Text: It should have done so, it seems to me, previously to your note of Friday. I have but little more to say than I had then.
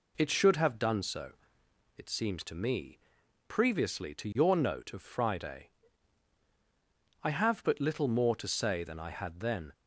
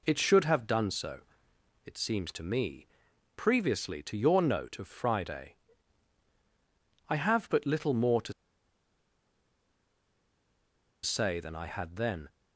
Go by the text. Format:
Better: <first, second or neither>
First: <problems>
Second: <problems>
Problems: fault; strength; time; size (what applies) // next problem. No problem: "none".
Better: first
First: none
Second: pauses between "to" and "say"; strong; at 8.3 s; 2.7 s long